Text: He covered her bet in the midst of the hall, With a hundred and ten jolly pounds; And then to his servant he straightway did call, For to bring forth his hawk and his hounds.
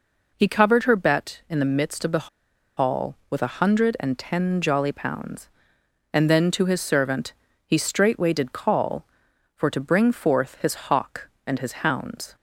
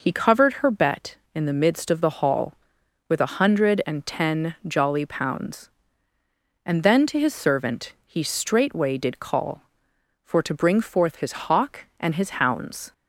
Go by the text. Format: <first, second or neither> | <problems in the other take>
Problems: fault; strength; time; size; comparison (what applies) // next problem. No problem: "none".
second | pauses between "the" and "hall"; noticeable; at 2.2 s; 0.49 s long // pauses between "servant" and "he"; slight; at 7.3 s; 0.32 s long